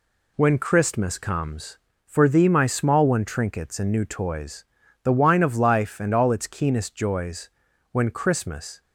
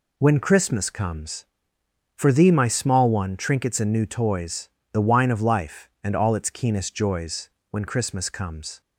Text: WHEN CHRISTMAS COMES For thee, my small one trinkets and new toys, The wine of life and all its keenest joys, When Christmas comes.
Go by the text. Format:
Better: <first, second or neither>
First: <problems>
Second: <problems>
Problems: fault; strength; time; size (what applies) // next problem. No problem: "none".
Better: second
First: stops before "comes"; at 8.7 s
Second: none